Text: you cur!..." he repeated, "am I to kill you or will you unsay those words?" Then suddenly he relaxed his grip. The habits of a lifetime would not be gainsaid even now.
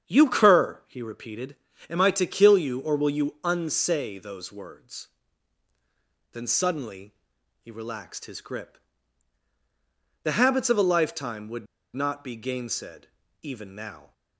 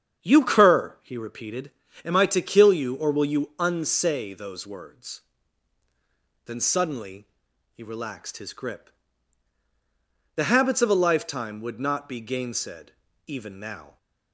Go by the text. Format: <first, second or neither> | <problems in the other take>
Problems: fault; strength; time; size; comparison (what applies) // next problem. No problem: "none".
second | starts louder than the rest; strong; until 1.1 s; 8 dB; strong in the second // pauses between "suddenly" and "he"; noticeable; at 7.1 s; 0.46 s long; also in the second // pauses between "would" and "not"; slight; at 11.6 s; 0.28 s long // pauses between "gainsaid" and "even"; slight; at 13.0 s; 0.34 s long; slight in the second